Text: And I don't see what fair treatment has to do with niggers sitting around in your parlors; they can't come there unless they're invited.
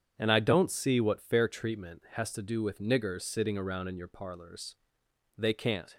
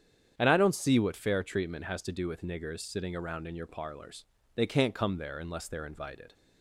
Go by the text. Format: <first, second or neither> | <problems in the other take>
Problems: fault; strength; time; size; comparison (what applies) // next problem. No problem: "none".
second | starts louder than the rest; strong; until 1.1 s; 8 dB; strong in the second // stops before "come there unless they're invited"; at 5.9 s